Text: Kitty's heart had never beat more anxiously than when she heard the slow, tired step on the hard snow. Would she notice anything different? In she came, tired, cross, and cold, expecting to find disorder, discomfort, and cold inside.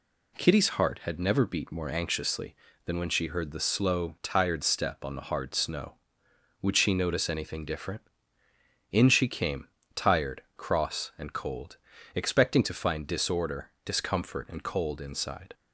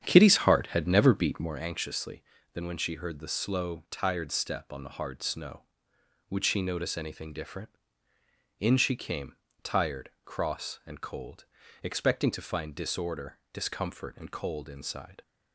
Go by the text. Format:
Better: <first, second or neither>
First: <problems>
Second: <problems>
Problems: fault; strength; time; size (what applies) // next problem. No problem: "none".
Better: first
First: none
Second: starts louder than the rest; strong; until 1.6 s; 9 dB